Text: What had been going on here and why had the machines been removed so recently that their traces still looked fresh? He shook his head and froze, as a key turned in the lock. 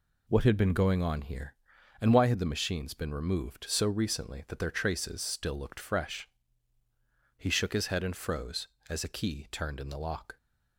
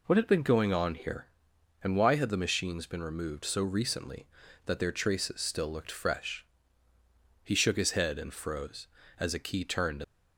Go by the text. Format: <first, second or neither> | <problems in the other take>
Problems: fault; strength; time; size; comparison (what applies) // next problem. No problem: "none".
first | stops before "in the lock"; at 10.0 s